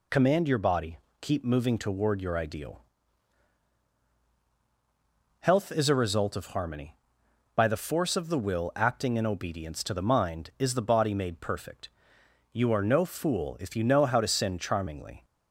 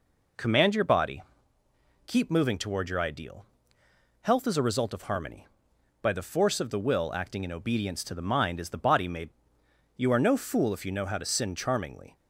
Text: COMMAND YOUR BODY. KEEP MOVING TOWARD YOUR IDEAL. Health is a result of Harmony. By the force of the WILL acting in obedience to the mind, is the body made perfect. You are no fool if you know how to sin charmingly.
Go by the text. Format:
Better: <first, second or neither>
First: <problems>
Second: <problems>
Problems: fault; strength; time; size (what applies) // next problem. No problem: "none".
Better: first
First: none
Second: skips "perfect"; at 9.6 s